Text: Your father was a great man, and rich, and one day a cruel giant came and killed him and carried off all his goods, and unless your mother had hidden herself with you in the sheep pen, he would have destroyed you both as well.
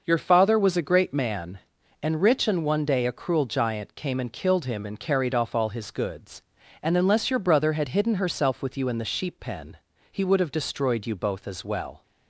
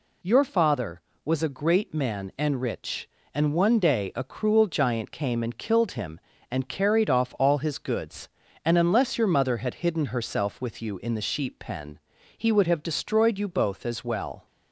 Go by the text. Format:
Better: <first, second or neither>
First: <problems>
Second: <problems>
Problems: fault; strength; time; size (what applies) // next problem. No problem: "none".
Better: second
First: says "brother" for "mother"; at 7.4 s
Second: none